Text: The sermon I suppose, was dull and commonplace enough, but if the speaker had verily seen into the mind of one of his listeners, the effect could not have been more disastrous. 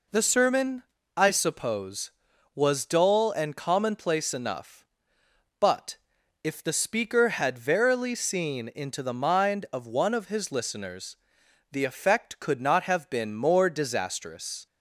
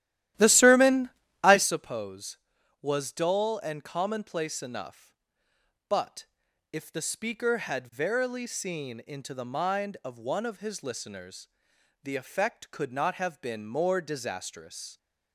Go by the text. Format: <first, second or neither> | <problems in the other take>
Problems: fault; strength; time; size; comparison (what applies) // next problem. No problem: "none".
first | starts louder than the rest; strong; until 1.8 s; 13 dB // pauses between "sermon" and "I"; slight; at 1.1 s; 0.34 s long; slight in the first // pauses between "but" and "if"; noticeable; at 6.2 s; 0.48 s long; noticeable in the first